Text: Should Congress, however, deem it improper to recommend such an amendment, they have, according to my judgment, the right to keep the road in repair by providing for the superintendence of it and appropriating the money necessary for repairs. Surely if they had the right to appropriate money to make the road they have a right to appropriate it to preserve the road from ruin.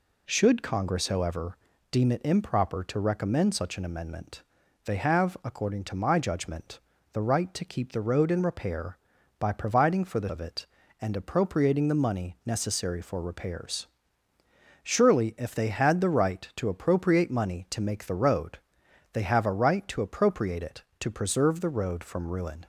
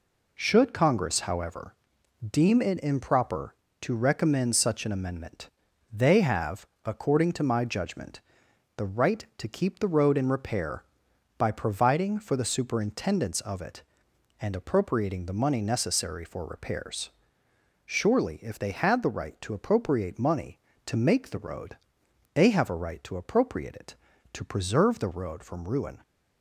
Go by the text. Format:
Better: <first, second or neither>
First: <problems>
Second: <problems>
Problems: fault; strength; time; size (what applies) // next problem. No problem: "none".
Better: second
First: skips "superintendence"; at 10.2 s // pauses between "road" and "they"; noticeable; at 18.5 s; 0.56 s long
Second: pauses between "road" and "they"; noticeable; at 21.7 s; 0.56 s long